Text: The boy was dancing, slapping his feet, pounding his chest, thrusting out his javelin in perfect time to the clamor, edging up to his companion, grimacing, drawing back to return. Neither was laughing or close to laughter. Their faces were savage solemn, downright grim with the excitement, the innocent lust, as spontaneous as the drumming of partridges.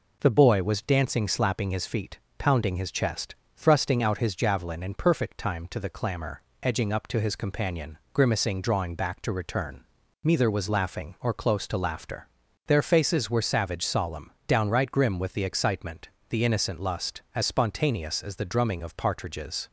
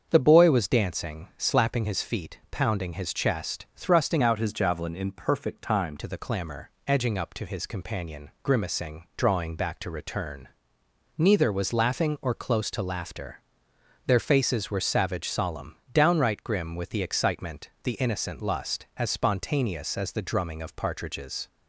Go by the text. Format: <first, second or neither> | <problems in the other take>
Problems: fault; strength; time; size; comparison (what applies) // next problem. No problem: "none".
first | starts louder than the rest; strong; until 1.1 s; 7 dB // changes voice from "out" to "time"; from 4.2 to 5.9 s; 1.7 s long